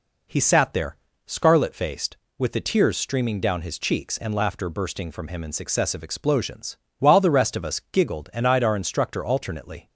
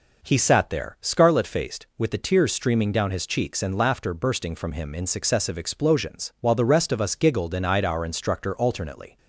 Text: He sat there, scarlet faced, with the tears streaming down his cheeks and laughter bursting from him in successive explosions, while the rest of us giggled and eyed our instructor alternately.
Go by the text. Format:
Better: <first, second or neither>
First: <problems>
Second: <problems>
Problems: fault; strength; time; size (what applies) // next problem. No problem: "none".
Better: neither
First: none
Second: none